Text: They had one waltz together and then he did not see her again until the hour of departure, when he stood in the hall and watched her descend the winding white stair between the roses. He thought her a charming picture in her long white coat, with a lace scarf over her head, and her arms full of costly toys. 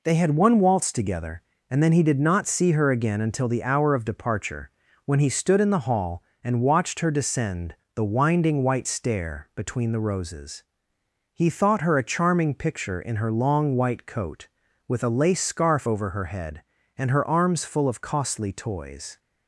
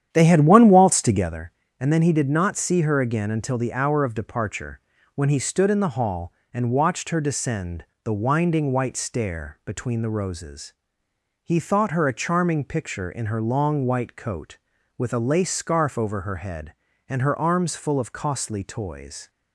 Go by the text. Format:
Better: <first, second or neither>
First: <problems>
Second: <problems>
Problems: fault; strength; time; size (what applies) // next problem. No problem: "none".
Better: first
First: pauses between "descend" and "the"; slight; at 7.7 s; 0.20 s long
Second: starts louder than the rest; strong; until 1.3 s; 9.5 dB // pauses between "descend" and "the"; slight; at 7.8 s; 0.19 s long